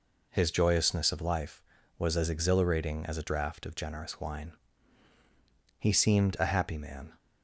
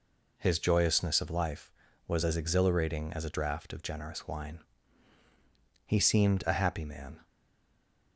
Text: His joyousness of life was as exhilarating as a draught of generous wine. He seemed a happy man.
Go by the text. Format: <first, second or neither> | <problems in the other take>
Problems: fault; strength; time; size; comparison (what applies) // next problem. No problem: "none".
first | stays silent after the last word; slight; from 7.2 s on; 0.9 s long